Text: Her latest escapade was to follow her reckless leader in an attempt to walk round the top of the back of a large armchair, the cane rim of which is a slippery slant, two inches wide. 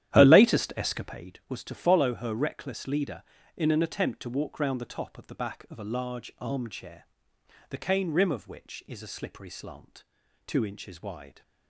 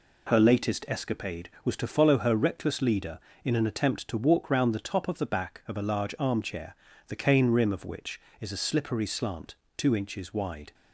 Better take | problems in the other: second | starts louder than the rest; strong; until 1.3 s; 11.5 dB

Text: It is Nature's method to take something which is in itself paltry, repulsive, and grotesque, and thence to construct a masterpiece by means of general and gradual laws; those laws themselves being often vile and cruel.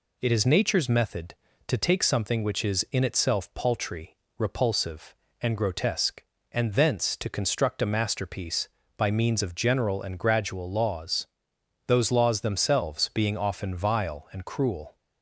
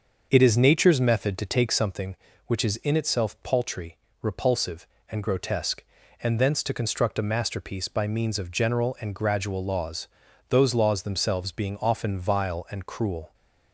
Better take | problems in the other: first | starts louder than the rest; until 2.0 s; 6.5 dB

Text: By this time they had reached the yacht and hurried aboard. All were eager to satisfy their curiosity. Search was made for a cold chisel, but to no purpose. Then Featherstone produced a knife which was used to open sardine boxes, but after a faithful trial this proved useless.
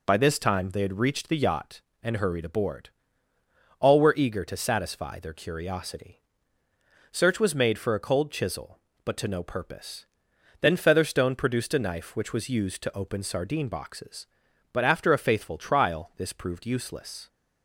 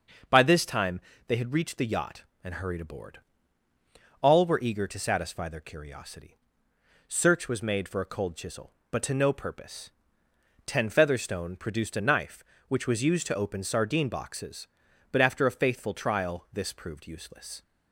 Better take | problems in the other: first | starts louder than the rest; until 1.5 s; 6.5 dB // pauses between "time" and "they"; slight; at 0.9 s; 0.28 s long // says "Ten" for "Then"; at 10.6 s

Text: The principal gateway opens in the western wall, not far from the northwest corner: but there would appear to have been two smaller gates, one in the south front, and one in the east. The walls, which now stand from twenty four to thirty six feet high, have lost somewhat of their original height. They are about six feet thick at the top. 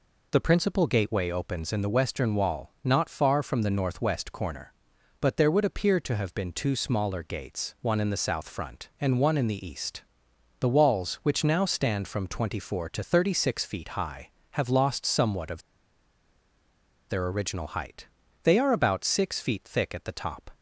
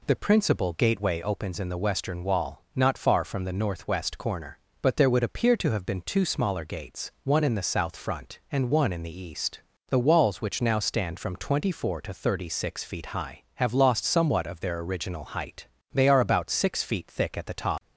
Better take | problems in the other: second | pauses between "of" and "their"; strong; at 15.6 s; 1.4 s long

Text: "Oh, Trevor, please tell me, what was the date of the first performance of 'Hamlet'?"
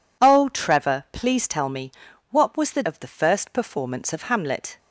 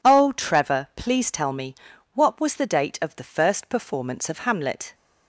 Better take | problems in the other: second | skips "date"; at 2.8 s

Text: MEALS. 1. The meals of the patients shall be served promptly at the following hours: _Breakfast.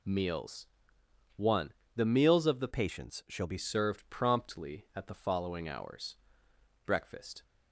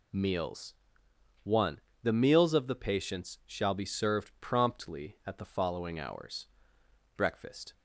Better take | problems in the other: second | changes voice from "patients" to "be"; from 2.7 to 3.5 s; 0.8 s long

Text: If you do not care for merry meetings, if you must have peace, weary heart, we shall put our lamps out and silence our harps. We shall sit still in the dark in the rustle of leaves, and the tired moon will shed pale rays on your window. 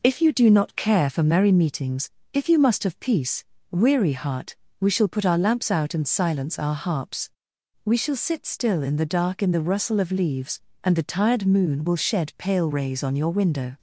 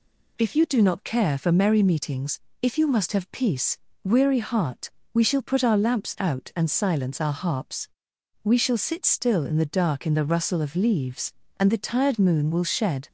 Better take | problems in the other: first | stops before "pale rays on your window"; at 13.0 s

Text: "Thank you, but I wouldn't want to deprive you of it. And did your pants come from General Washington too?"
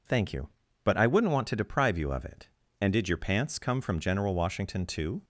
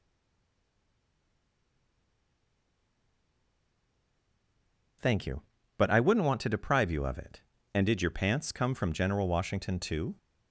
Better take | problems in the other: first | stays silent before the first word; strong; until 5.0 s; 5.0 s long

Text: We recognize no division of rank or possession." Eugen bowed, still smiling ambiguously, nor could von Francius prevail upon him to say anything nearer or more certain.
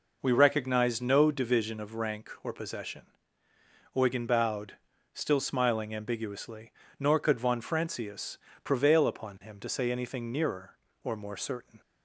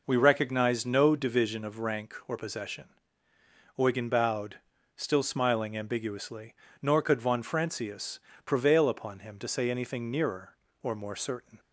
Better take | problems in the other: neither | pauses between "Francius" and "prevail"; slight; the same in both

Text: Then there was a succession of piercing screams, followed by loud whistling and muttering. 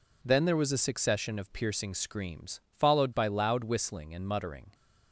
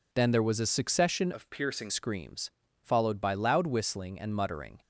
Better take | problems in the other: first | changes voice from "of" to "piercing"; from 1.3 to 1.8 s; 0.5 s long

